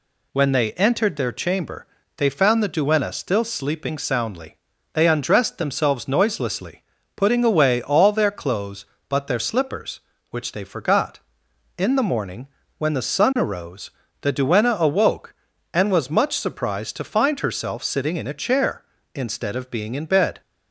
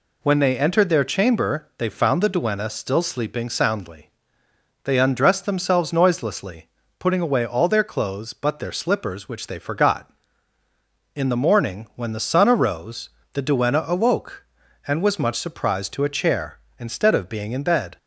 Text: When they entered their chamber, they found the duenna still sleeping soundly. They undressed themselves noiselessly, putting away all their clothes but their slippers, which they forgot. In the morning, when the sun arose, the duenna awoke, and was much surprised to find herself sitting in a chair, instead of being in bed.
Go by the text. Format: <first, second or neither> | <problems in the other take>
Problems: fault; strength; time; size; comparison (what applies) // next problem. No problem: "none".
first | skips "find herself sitting in"; at 16.0 s